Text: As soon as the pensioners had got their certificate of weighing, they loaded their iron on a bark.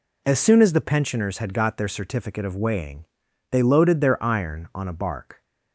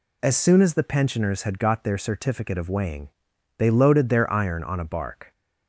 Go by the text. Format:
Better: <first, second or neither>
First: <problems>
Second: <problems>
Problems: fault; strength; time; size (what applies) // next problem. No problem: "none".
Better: neither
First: none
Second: none